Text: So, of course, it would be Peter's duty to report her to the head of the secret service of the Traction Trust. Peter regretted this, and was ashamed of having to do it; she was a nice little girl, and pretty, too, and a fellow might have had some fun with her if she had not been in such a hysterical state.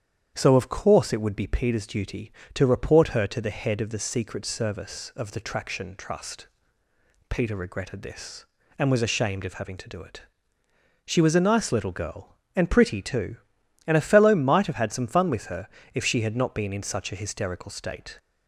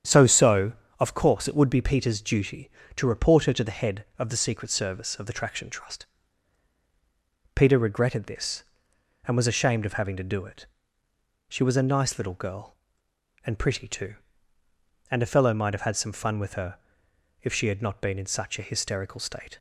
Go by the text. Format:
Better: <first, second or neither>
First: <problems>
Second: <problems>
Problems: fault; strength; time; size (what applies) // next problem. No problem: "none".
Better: first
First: starts louder than the rest; strong; until 1.3 s; 9 dB // pauses between "her" and "if"; slight; at 15.6 s; 0.26 s long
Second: starts louder than the rest; strong; until 1.3 s; 8.5 dB // says "So" twice; at 0.2 s // pauses between "her" and "if"; noticeable; at 16.7 s; 0.64 s long